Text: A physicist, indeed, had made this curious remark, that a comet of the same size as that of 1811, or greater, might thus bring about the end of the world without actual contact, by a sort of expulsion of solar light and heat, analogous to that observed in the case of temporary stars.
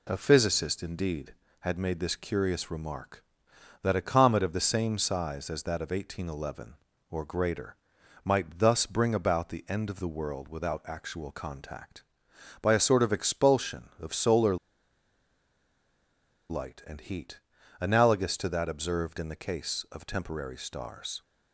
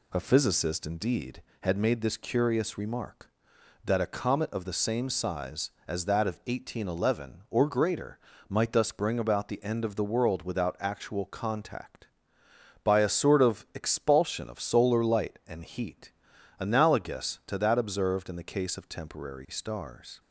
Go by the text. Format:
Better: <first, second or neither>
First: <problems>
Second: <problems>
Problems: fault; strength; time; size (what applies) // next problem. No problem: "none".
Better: second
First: pauses between "solar" and "light"; strong; at 14.5 s; 1.9 s long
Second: none